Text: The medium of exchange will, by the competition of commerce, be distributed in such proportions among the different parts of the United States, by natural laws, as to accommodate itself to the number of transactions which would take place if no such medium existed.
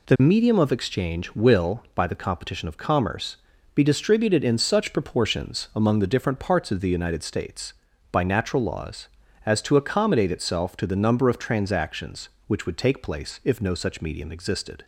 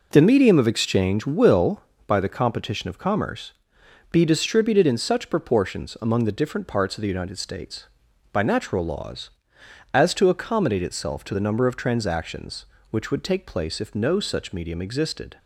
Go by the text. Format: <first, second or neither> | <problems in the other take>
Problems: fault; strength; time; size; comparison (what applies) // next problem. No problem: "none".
first | starts louder than the rest; noticeable; until 1.9 s; 4.5 dB